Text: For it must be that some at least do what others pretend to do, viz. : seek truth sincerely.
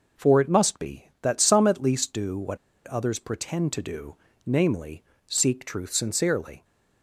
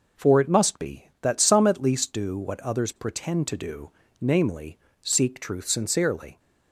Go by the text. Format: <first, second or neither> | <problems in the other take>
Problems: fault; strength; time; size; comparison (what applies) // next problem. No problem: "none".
second | pauses between "what" and "others"; slight; at 2.5 s; 0.30 s long